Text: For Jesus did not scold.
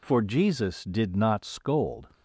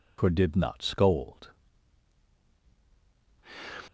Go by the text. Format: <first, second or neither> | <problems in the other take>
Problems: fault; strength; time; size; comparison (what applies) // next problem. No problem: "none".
first | skips "Jesus"; at 0.2 s